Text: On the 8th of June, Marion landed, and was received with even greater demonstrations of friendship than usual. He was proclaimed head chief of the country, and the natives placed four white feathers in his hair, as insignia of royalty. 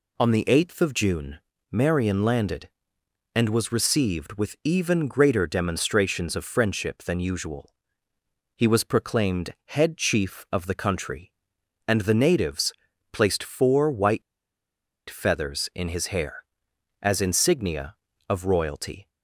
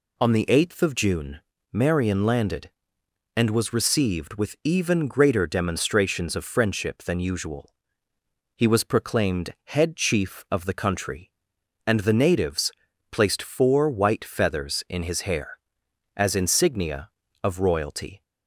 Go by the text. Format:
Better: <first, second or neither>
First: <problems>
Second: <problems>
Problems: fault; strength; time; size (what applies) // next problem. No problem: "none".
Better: second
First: pauses between "natives" and "placed"; at 12.7 s; 0.40 s long // pauses between "white" and "feathers"; noticeable; at 14.2 s; 0.87 s long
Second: pauses between "natives" and "placed"; at 12.7 s; 0.40 s long